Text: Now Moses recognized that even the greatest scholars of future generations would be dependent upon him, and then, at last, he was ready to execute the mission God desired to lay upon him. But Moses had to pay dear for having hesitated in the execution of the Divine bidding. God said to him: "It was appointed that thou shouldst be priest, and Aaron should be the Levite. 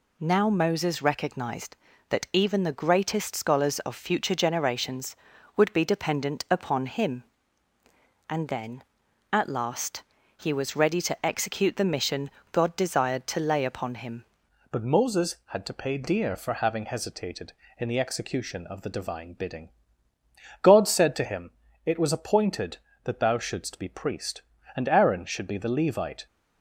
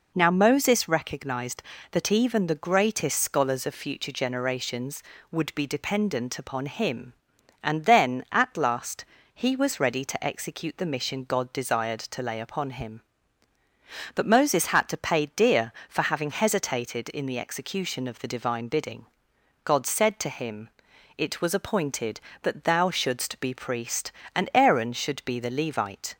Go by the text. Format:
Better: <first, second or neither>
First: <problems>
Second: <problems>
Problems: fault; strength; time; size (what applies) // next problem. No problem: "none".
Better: second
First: pauses between "mission" and "God"; slight; at 12.3 s; 0.22 s long // changes voice at "But"; from 14.7 s on; 11.5 s long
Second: none